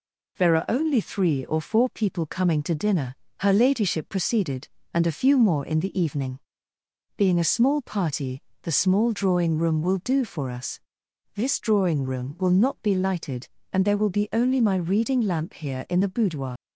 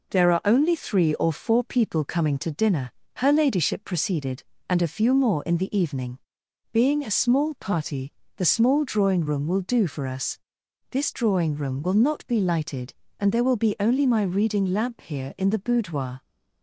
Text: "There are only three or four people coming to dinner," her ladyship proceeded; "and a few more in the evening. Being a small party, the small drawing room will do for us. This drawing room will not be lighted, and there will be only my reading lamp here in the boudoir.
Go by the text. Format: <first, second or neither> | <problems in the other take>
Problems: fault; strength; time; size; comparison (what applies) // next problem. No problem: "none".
second | leaves "boudoir" unfinished; at 16.5 s; 105 ms